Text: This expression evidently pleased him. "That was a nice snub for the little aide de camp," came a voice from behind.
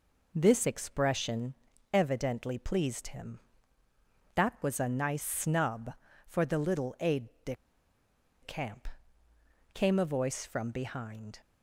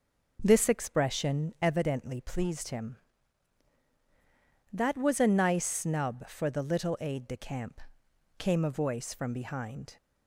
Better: second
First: pauses between "expression" and "evidently"; at 1.5 s; 0.40 s long // pauses between "aide" and "de"; slight; at 7.2 s; 0.16 s long // pauses between "de" and "camp"; noticeable; at 7.5 s; 0.87 s long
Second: none

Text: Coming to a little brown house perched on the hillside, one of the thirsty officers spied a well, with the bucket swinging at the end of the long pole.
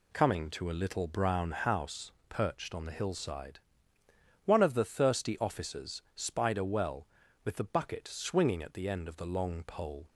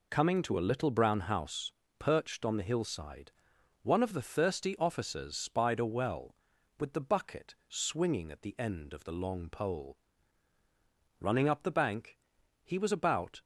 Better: first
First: pauses between "house" and "perched"; slight; at 2.1 s; 0.18 s long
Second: pauses between "house" and "perched"; slight; at 1.7 s; 0.28 s long // goes on to say "Running up the bank he was about"; strong; from 11.2 s on; 2.2 s long

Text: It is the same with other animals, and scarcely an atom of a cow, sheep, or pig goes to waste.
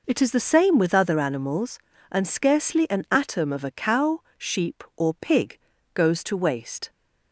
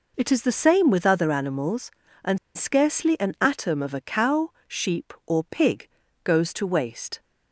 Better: first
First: pauses between "pig" and "goes"; slight; at 5.5 s; 0.34 s long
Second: pauses between "and" and "scarcely"; slight; at 2.3 s; 0.18 s long // pauses between "pig" and "goes"; slight; at 5.8 s; 0.34 s long

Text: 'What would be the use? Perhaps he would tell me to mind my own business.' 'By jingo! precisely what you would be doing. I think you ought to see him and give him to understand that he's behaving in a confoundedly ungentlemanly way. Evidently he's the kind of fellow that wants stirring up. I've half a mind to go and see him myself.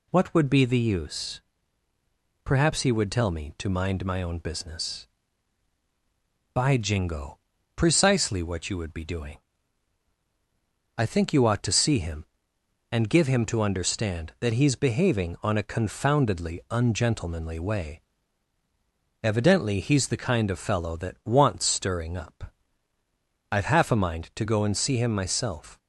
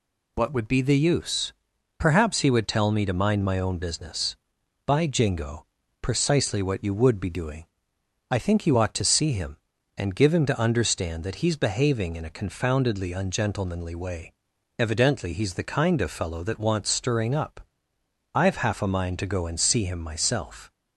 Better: second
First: says "on" for "in"; at 15.4 s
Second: none

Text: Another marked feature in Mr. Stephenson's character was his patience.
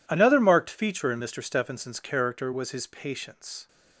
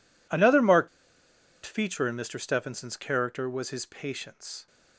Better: first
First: none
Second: pauses between "marked" and "feature"; noticeable; at 0.8 s; 0.75 s long

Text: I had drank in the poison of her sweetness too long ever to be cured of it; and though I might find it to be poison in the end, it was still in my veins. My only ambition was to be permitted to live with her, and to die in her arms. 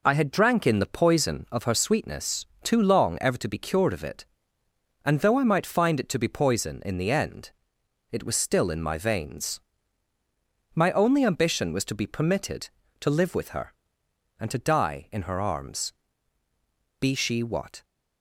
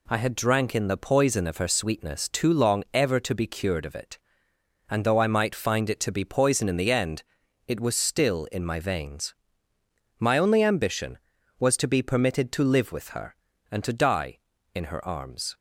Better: second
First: pauses between "sweetness" and "too"; slight; at 2.4 s; 0.18 s long // goes on to say "Be she what"; noticeable; from 16.9 s on; 0.84 s long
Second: none

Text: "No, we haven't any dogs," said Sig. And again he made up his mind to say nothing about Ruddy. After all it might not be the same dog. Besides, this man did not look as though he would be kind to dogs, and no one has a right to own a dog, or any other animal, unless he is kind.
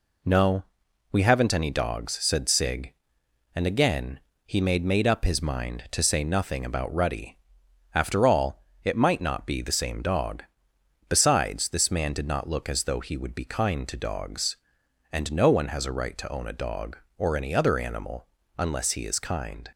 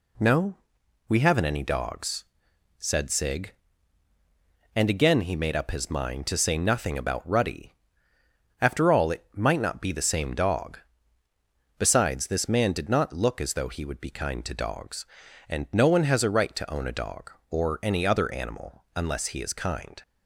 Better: second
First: pauses between "again" and "he"; slight; at 4.1 s; 0.24 s long // says "made" twice; at 4.8 s // pauses between "all" and "it"; slight; at 8.5 s; 0.24 s long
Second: none

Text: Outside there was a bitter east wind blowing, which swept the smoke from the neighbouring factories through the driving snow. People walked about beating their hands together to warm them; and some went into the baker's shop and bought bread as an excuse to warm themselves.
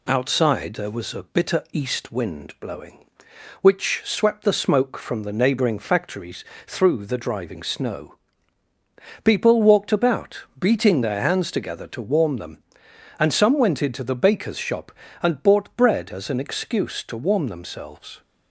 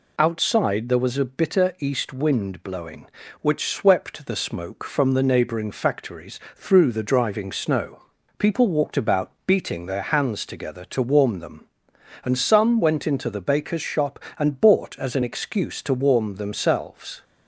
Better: first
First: pauses between "factories" and "through"; slight; at 6.4 s; 0.24 s long // pauses between "about" and "beating"; slight; at 10.4 s; 0.16 s long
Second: pauses between "factories" and "through"; slight; at 6.3 s; 0.16 s long // pauses between "about" and "beating"; slight; at 9.3 s; 0.16 s long // skips "bread"; at 14.9 s

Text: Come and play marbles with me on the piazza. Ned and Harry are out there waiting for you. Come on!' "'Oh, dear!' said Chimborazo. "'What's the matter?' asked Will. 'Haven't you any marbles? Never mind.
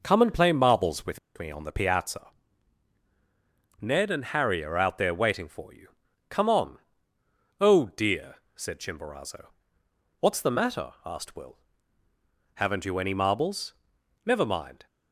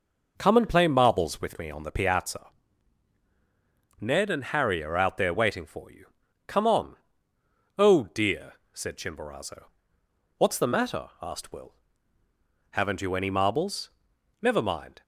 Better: second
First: pauses between "with" and "me"; slight; at 1.1 s; 0.18 s long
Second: none

